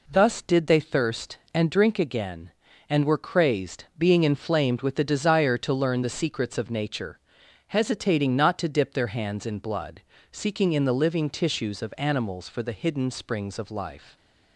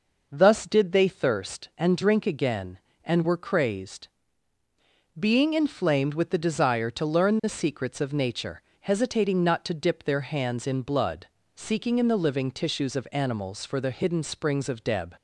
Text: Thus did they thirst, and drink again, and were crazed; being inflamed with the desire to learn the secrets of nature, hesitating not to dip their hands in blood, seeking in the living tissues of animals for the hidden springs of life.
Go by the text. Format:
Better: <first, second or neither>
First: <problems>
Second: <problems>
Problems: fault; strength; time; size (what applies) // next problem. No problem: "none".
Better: first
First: none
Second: says "deb" for "life"; at 14.8 s